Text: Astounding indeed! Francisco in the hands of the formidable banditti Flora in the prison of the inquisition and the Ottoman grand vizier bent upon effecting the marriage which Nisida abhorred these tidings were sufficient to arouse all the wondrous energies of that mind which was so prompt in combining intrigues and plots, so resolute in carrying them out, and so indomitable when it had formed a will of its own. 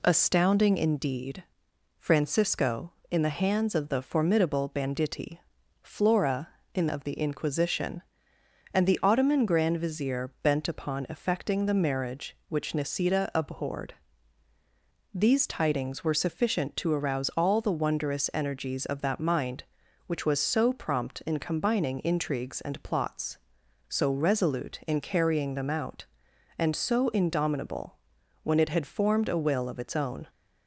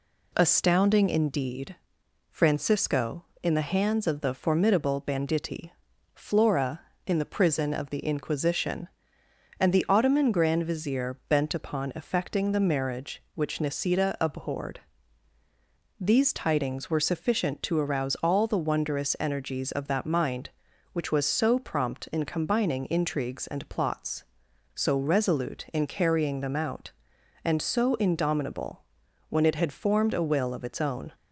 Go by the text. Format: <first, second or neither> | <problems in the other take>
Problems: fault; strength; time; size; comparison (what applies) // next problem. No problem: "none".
second | pauses between "banditti" and "Flora"; at 5.3 s; 0.44 s long; also in the second // skips "the prison"; at 6.8 s // pauses between "abhorred" and "these"; at 13.9 s; 1.2 s long; also in the second // pauses between "indomitable" and "when"; noticeable; at 27.9 s; 0.46 s long; noticeable in the second